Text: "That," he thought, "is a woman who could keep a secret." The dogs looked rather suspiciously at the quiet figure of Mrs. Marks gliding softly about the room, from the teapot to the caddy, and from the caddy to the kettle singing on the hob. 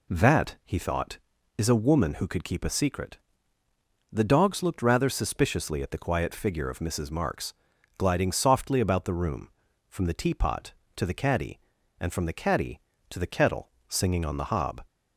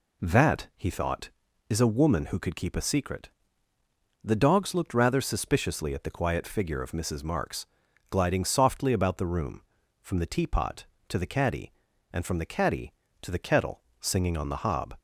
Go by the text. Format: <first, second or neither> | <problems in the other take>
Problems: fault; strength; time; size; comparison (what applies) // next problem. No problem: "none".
neither | pauses between "Marks" and "gliding"; noticeable; the same in both // pauses between "kettle" and "singing"; slight; the same in both